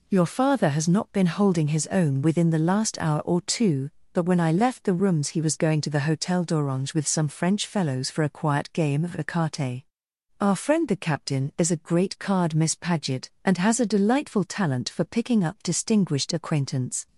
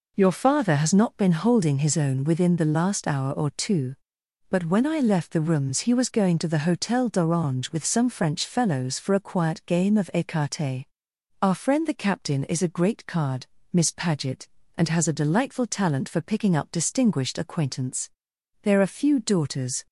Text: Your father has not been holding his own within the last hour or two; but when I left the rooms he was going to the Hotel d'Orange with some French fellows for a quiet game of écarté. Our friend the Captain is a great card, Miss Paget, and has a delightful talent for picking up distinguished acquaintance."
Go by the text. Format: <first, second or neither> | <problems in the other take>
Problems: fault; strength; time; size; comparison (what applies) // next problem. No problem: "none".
first | goes on to say "There are few daughters"; noticeable; from 18.6 s on; 1.2 s long